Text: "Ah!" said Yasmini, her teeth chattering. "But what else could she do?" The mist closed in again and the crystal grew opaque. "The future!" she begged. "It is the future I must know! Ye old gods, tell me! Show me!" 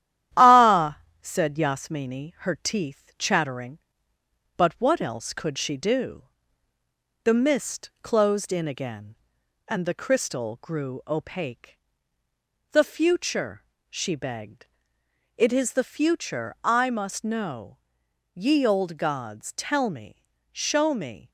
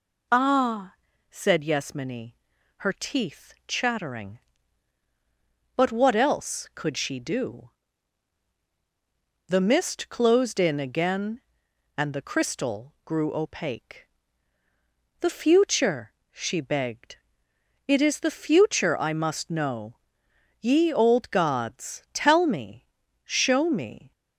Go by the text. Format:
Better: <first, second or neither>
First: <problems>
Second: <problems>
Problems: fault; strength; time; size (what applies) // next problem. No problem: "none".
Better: second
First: gets quieter; noticeable; throughout; 4 dB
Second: none